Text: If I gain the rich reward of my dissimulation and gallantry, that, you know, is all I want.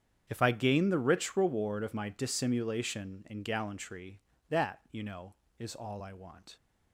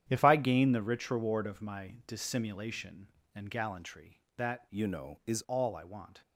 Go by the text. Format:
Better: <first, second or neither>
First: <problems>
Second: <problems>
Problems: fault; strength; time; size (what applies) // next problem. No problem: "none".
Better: first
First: starts louder than the rest; strong; until 1.3 s; 8.5 dB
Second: starts louder than the rest; strong; until 1.1 s; 10 dB // changes voice from "you" to "is"; from 4.6 to 5.4 s; 0.8 s long